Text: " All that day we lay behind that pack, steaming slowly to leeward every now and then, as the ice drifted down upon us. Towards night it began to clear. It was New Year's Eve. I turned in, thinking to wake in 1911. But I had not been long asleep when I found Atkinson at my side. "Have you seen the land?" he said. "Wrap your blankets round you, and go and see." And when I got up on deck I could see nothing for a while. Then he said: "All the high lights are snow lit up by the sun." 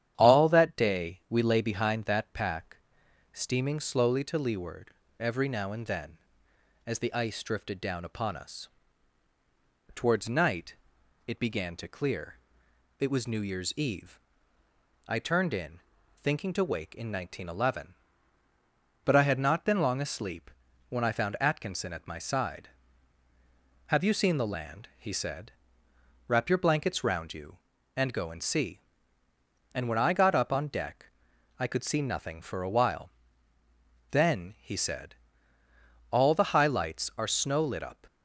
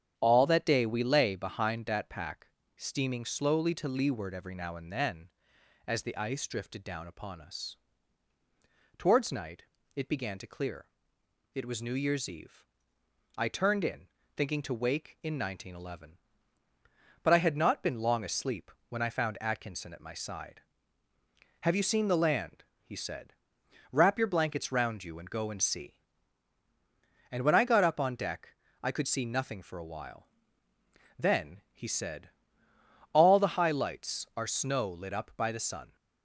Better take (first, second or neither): second